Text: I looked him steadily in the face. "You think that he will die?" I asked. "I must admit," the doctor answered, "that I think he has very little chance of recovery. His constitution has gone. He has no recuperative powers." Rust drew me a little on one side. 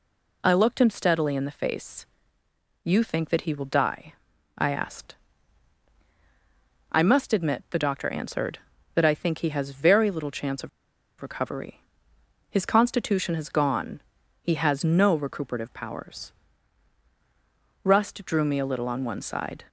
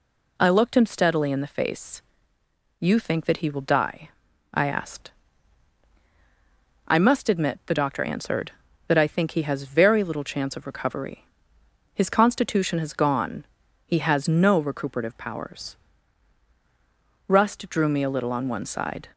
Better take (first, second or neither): second